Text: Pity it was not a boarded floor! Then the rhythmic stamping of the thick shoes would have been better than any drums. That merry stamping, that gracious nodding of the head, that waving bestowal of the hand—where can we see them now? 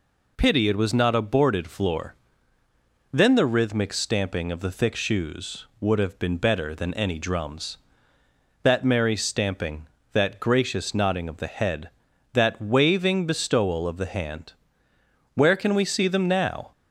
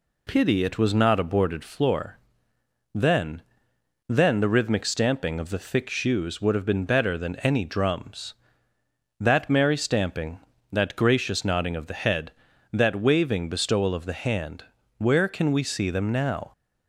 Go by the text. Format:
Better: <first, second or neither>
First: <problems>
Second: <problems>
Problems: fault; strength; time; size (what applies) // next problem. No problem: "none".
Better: first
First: none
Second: says "Then" twice; at 4.0 s